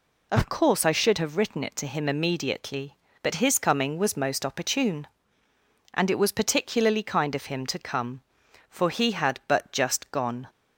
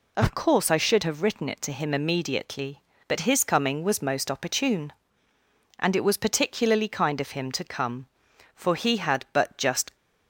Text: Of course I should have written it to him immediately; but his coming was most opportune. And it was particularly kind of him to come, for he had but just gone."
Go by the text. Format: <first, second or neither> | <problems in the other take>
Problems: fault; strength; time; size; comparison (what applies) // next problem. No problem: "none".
first | stops before "gone"; at 9.9 s